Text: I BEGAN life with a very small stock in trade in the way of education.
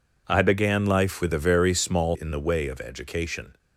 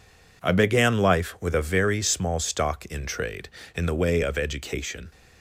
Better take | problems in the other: second | skips "stock in trade"; at 2.1 s

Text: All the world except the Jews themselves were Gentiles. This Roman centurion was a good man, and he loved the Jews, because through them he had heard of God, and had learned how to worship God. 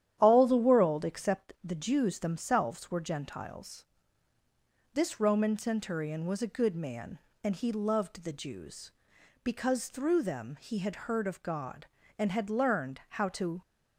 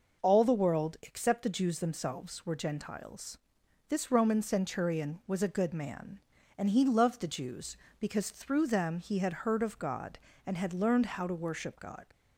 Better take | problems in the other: second | starts louder than the rest; strong; until 1.2 s; 10.5 dB // stops before "worship God"; at 13.6 s

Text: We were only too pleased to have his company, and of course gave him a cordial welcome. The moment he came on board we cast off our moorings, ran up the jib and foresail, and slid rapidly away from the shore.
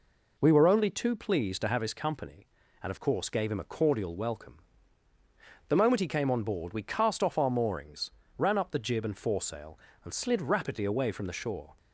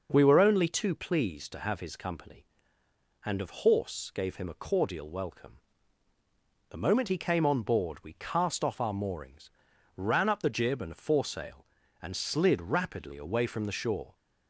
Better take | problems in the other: first | says "horse" for "course"; at 3.6 s

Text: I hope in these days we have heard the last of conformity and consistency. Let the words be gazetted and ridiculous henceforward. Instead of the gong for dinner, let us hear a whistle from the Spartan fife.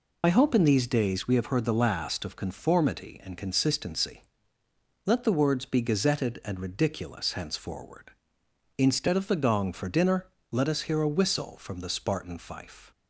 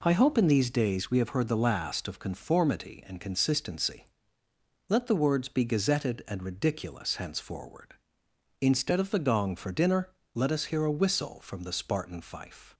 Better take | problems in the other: second | loses the start of "I"; at 0.2 s; 60 ms

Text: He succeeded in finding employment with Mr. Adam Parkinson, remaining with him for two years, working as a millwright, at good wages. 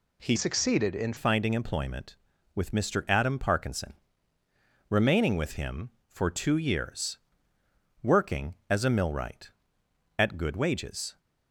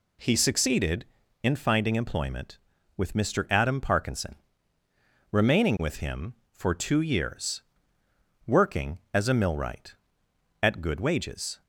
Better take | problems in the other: second | changes voice from "succeeded" to "in"; from 0.3 to 1.1 s; 0.8 s long

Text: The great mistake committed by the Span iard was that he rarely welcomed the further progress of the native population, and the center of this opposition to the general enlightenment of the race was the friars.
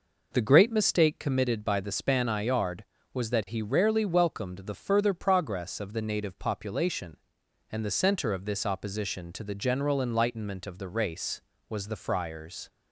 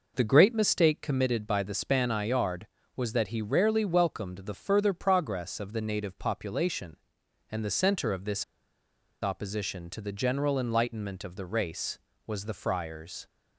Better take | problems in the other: first | pauses between "this" and "opposition"; noticeable; at 8.4 s; 0.78 s long

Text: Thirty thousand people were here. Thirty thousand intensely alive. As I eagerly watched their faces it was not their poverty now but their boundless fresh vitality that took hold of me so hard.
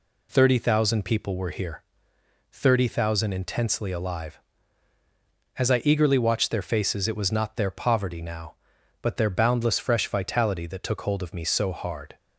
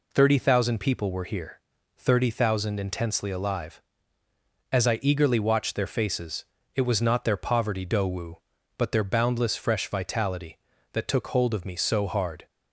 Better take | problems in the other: first | pauses between "faces" and "it"; slight; at 6.4 s; 0.30 s long // says "dowu" for "now"; at 7.8 s

